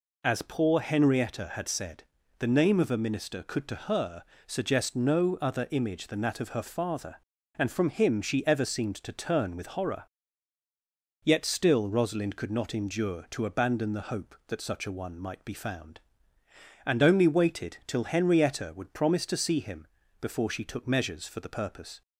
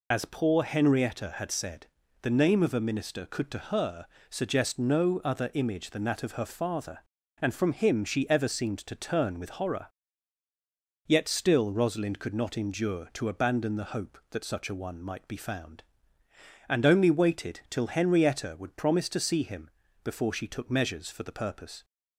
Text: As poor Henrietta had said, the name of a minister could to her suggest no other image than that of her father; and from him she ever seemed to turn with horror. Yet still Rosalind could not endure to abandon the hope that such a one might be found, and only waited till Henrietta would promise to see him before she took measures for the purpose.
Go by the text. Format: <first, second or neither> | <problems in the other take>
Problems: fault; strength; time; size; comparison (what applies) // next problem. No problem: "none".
first | loses the start of "As"; at 0.1 s; 40 ms // pauses between "her" and "suggest"; slight; at 4.0 s; 0.24 s long; slight in the first // pauses between "him" and "before"; slight; at 19.7 s; 0.32 s long; slight in the first